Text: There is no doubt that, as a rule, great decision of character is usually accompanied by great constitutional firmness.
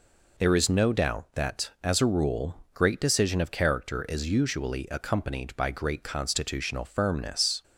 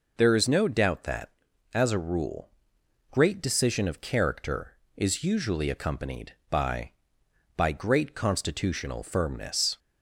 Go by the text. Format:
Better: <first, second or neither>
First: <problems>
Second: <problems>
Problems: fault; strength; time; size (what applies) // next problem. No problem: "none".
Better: first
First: none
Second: says "by" twice; at 7.5 s